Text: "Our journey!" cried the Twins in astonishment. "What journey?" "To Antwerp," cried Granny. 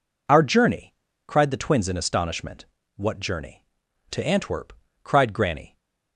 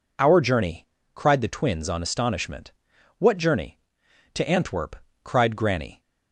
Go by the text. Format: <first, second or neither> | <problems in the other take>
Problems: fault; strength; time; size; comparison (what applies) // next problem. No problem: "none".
first | says "on" for "in"; at 1.8 s